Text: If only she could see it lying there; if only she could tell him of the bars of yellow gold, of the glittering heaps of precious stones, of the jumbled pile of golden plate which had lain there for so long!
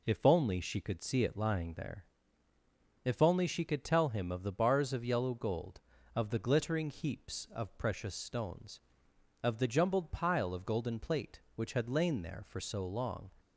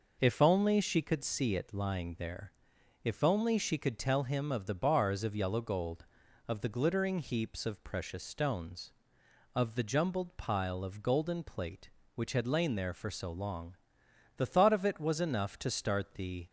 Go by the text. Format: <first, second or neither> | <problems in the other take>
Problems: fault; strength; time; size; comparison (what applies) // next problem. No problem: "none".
first | goes on to say "The thought of it was enough to start the"; strong; from 14.3 s on; 2.1 s long